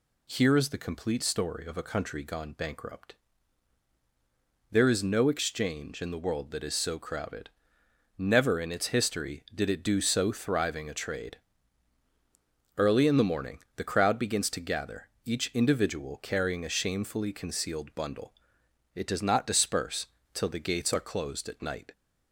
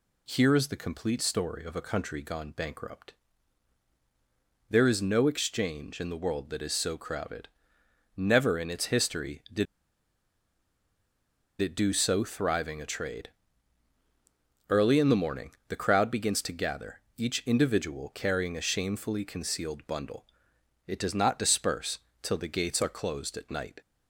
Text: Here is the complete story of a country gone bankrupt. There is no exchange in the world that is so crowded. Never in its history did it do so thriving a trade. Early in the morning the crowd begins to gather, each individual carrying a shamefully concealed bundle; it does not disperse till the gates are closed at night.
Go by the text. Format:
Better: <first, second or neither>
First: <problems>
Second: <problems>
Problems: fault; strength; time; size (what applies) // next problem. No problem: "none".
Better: first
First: pauses between "morning" and "the"; slight; at 13.5 s; 0.18 s long // pauses between "disperse" and "till"; slight; at 20.0 s; 0.25 s long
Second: pauses between "did" and "it"; strong; at 9.6 s; 1.9 s long // pauses between "morning" and "the"; slight; at 15.5 s; 0.18 s long // pauses between "disperse" and "till"; slight; at 21.9 s; 0.22 s long